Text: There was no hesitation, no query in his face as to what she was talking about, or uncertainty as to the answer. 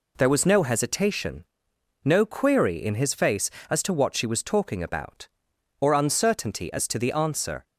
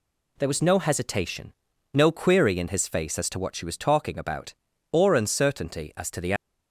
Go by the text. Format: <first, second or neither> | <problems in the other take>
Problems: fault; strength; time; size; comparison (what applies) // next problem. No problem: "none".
first | stops before "answer"; at 6.3 s